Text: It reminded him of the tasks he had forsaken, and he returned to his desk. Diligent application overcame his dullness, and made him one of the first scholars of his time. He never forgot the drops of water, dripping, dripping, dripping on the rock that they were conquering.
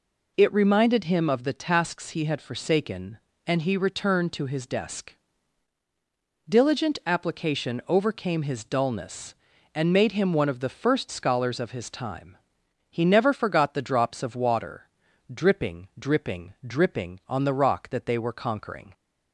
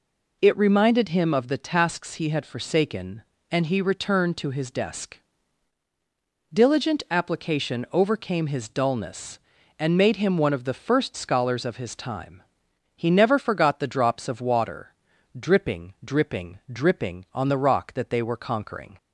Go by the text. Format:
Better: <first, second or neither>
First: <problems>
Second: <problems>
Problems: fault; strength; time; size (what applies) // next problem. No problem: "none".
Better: neither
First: none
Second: none